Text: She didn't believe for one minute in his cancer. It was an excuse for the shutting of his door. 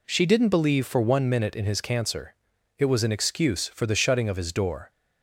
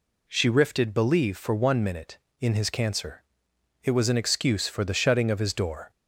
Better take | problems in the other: first | says "rifted" for "didn't"; at 0.4 s

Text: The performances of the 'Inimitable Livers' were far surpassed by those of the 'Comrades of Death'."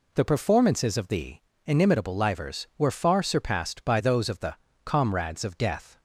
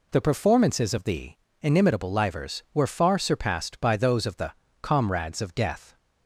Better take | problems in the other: neither | pauses between "the" and "Inimitable"; slight; the same in both // pauses between "the" and "Comrades"; slight; the same in both

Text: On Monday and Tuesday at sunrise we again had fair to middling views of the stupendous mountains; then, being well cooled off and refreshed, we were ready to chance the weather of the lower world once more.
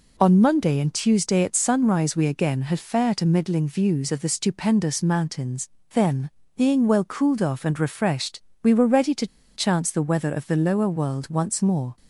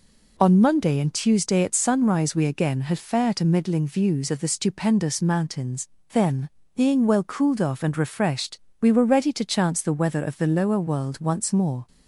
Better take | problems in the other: second | pauses between "to" and "chance"; slight; at 9.2 s; 0.29 s long

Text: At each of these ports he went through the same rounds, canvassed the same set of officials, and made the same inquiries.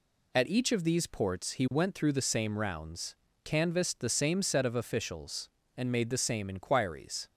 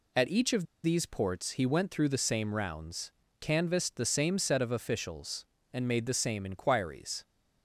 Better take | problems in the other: first | pauses between "of" and "these"; slight; at 0.6 s; 0.19 s long

